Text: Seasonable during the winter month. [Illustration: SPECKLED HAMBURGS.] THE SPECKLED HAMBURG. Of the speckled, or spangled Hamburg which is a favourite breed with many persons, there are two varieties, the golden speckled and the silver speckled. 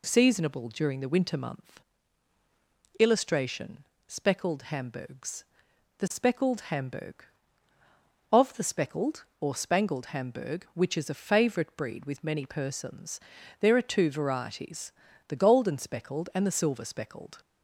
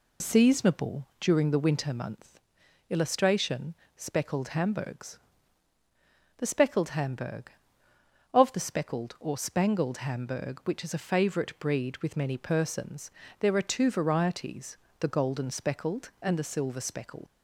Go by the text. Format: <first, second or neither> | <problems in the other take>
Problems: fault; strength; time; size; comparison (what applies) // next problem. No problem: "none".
first | leaves "speckled" unfinished; at 17.2 s; 105 ms